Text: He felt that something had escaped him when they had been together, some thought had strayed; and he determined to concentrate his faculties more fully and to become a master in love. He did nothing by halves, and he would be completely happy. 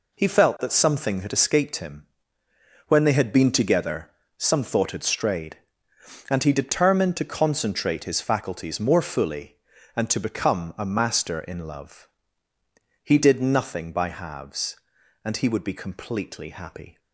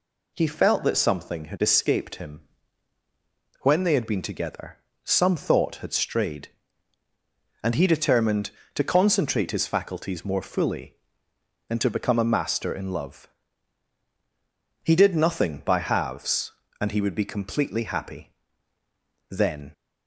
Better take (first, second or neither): first